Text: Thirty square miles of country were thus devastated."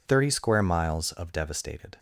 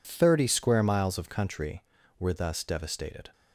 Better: second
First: skips "country were thus"; at 1.3 s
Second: none

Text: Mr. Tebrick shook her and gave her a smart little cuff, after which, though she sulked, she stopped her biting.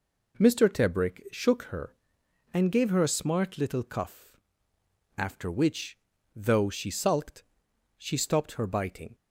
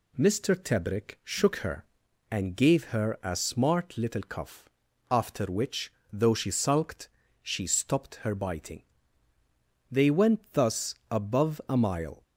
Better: first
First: none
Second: goes on to say "They went thus above a mile"; strong; from 9.9 s on; 2.3 s long

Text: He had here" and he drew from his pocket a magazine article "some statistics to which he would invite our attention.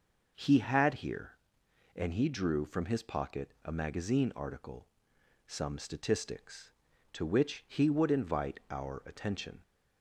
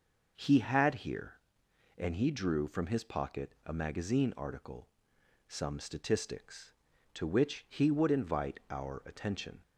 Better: neither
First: pauses between "article" and "some"; noticeable; at 4.8 s; 0.58 s long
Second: pauses between "article" and "some"; noticeable; at 4.8 s; 0.58 s long

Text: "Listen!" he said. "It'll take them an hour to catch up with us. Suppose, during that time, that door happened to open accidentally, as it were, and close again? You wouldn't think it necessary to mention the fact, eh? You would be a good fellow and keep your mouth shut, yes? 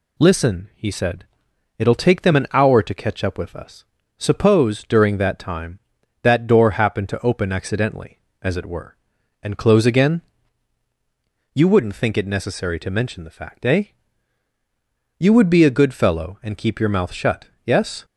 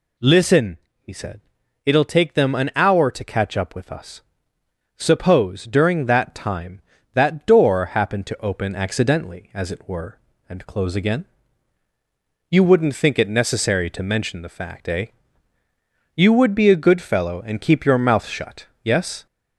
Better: first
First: none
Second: gets louder; slight; throughout; 3 dB

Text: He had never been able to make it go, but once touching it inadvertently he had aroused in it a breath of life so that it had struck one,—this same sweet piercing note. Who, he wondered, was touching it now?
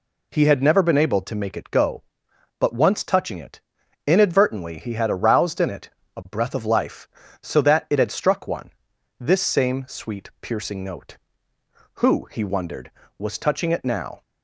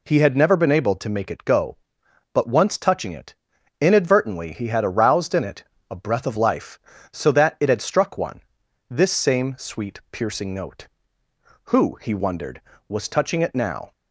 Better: neither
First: pauses between "it" and "inadvertently"; at 3.6 s; 0.44 s long // pauses between "it" and "a"; slight; at 5.8 s; 0.28 s long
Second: pauses between "it" and "inadvertently"; at 3.3 s; 0.44 s long // pauses between "it" and "a"; slight; at 5.6 s; 0.28 s long

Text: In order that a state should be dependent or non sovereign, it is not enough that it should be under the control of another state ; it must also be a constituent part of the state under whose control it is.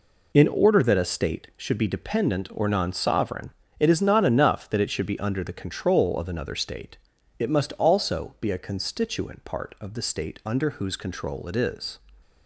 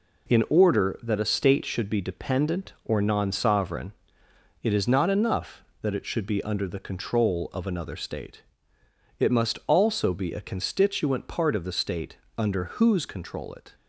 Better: first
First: none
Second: pauses between "state" and "under"; slight; at 12.1 s; 0.18 s long // stops before "is"; at 13.7 s

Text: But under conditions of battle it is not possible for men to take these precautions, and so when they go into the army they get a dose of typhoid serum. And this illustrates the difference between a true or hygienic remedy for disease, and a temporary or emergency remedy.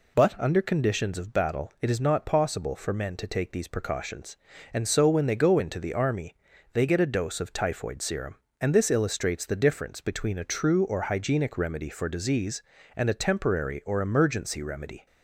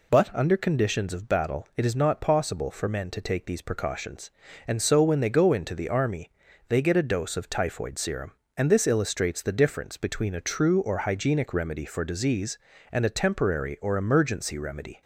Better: neither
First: pauses between "army" and "they"; at 6.3 s; 0.38 s long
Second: pauses between "army" and "they"; at 6.2 s; 0.38 s long

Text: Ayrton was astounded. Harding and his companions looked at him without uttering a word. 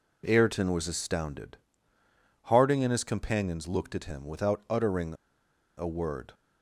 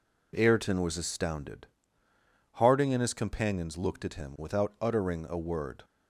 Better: second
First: pauses between "uttering" and "a"; noticeable; at 5.1 s; 0.63 s long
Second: none

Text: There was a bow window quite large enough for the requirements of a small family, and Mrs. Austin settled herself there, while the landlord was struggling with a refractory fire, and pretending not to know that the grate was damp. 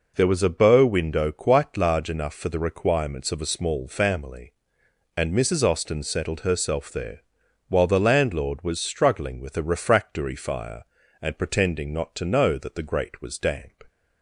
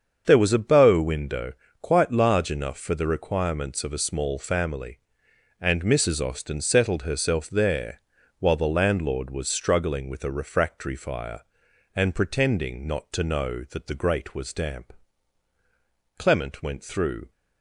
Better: first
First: none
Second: starts louder than the rest; until 1.2 s; 7 dB // pauses between "window" and "quite"; slight; at 1.5 s; 0.28 s long // goes on to say "Clement went through"; noticeable; from 16.1 s on; 1.1 s long

